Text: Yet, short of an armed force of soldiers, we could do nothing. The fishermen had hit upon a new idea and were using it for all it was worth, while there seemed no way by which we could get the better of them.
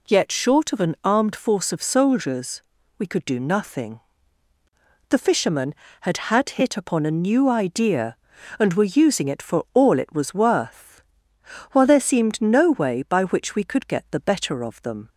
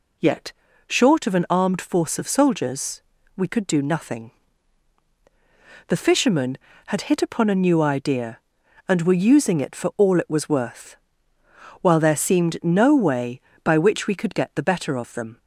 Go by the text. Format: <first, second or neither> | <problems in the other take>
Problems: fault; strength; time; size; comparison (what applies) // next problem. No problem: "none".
second | says "had" twice; at 6.2 s